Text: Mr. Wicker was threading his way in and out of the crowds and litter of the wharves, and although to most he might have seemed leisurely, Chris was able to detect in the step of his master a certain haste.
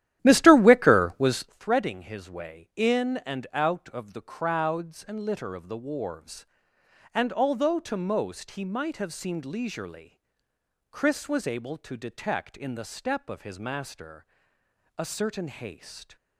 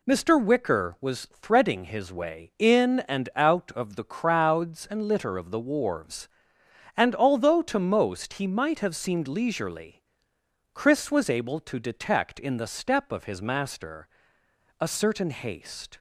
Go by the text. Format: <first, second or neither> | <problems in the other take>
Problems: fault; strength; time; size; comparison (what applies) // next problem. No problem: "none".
second | starts louder than the rest; strong; until 1.6 s; 12.5 dB // pauses between "master" and "a"; noticeable; at 14.2 s; 0.72 s long; noticeable in the second